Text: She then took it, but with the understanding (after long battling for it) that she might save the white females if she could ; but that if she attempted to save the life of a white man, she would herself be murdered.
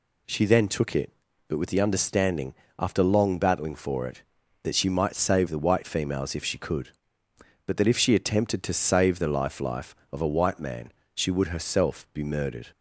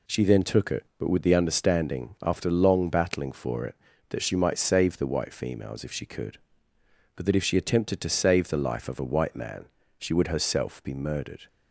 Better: second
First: says "life" twice; at 9.5 s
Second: none

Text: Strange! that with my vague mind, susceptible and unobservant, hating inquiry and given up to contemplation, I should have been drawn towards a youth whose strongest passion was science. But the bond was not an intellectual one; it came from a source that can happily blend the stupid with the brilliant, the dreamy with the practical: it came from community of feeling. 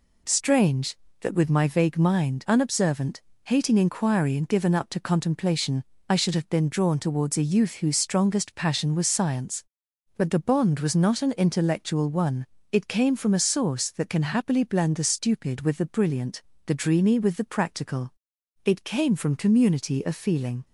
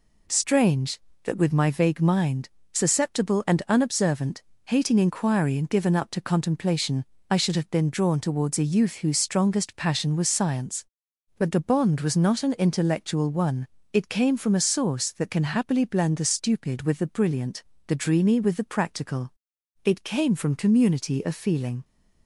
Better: second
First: skips "susceptible and"; at 2.4 s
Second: none

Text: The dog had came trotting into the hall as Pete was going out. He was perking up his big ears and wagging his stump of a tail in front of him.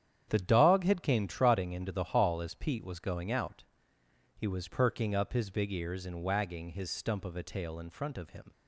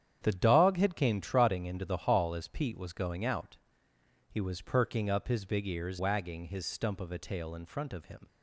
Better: first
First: starts louder than the rest; strong; until 1.3 s; 9 dB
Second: starts louder than the rest; strong; until 1.2 s; 9 dB // skips "and"; at 5.9 s

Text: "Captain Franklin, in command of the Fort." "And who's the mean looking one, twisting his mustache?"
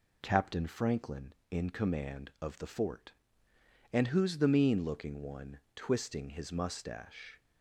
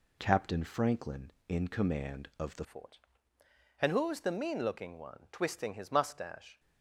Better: first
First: none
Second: changes voice at "Fort"; from 2.6 s on; 3.9 s long

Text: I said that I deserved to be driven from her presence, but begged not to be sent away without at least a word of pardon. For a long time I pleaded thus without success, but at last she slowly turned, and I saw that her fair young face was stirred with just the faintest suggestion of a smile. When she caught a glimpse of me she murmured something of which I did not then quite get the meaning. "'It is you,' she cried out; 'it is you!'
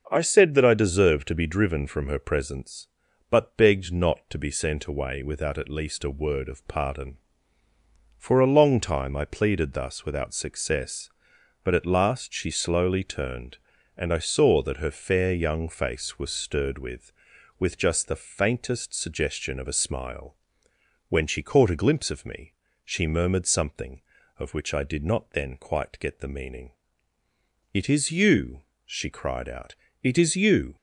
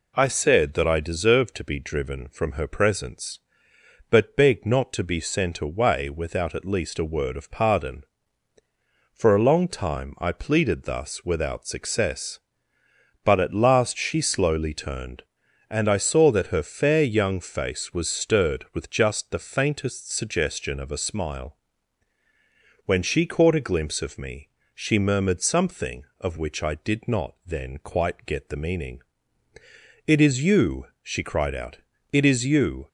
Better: second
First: starts louder than the rest; noticeable; until 1.1 s; 6 dB // says "with" twice; at 17.5 s // pauses between "me" and "she"; slight; at 22.5 s; 0.32 s long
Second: pauses between "me" and "she"; slight; at 24.4 s; 0.26 s long

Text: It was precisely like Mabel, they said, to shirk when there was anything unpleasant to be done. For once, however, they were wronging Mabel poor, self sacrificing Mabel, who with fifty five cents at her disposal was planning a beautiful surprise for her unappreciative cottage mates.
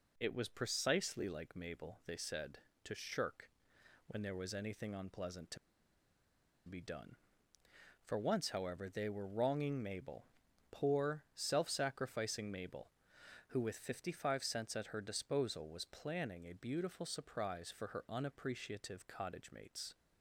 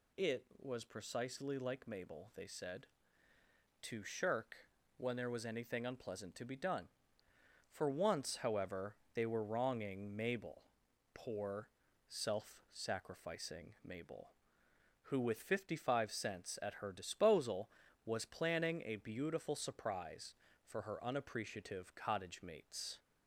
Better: second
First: pauses between "shirk" and "when"; noticeable; at 3.4 s; 0.58 s long // pauses between "to" and "be"; at 5.5 s; 1.1 s long // pauses between "Mabel" and "poor"; noticeable; at 10.2 s; 0.46 s long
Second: pauses between "shirk" and "when"; at 4.5 s; 0.44 s long // pauses between "Mabel" and "poor"; noticeable; at 10.6 s; 0.54 s long

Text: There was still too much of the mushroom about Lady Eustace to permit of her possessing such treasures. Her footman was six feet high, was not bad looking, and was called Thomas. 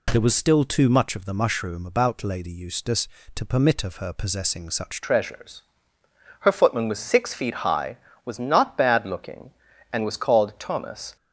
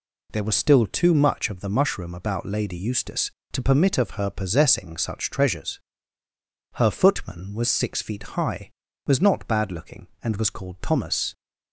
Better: second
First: changes voice at "treasures"; from 5.0 s on; 6.1 s long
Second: none

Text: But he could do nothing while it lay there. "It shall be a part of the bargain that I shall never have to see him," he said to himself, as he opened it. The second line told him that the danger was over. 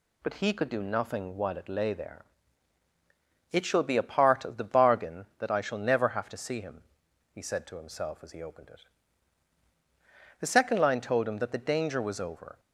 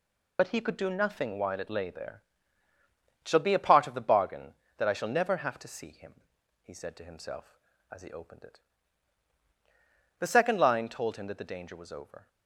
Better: first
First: none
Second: loses the start of "But"; at 0.3 s; 60 ms

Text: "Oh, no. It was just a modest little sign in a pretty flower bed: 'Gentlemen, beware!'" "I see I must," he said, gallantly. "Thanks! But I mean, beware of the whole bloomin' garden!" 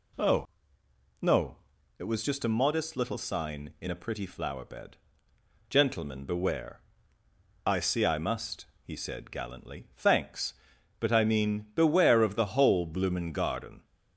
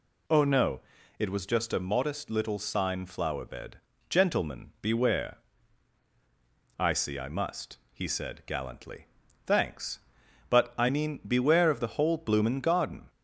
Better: first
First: none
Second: skips "in a pretty"; at 3.0 s

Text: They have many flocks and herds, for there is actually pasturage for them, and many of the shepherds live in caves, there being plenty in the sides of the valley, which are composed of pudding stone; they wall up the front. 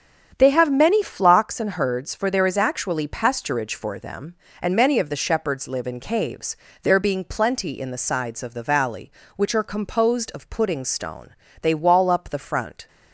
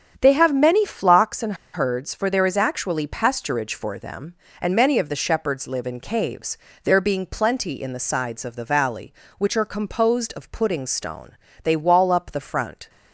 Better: first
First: starts louder than the rest; strong; until 1.4 s; 8 dB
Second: starts louder than the rest; strong; until 1.2 s; 8 dB // pauses between "and" and "herds"; slight; at 1.5 s; 0.19 s long

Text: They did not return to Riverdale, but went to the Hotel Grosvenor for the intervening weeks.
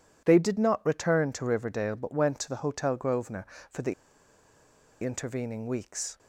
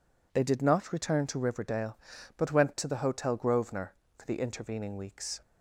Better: second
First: pauses between "the" and "intervening"; at 3.9 s; 1.1 s long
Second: none

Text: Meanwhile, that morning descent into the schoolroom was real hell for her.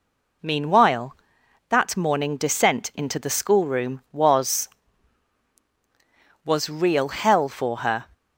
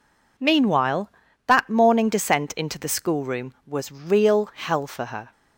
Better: second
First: says "was" twice; at 6.4 s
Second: none

